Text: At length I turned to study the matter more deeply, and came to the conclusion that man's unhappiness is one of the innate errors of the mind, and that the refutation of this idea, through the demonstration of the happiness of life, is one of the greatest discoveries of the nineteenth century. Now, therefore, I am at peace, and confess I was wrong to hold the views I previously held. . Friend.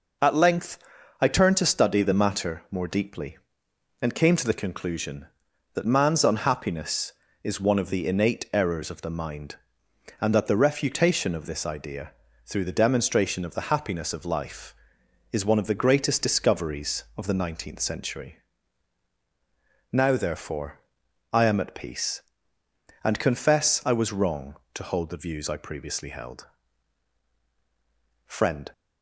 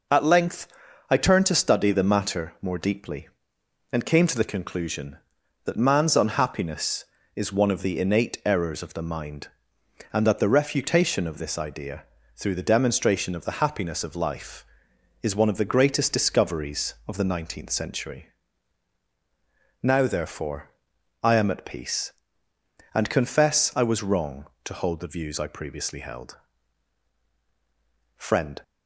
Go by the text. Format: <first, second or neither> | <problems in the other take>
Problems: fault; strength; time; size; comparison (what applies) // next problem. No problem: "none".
neither | pauses between "length" and "I"; the same in both